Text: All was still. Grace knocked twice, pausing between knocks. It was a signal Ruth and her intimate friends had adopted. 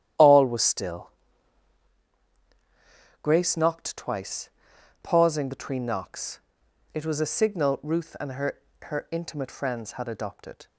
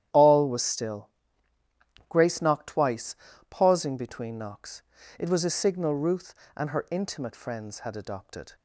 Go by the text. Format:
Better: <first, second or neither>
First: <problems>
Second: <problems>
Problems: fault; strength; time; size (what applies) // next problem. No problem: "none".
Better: second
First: starts louder than the rest; strong; until 3.3 s; 11 dB // says "her" twice; at 8.8 s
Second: starts louder than the rest; strong; until 2.1 s; 11 dB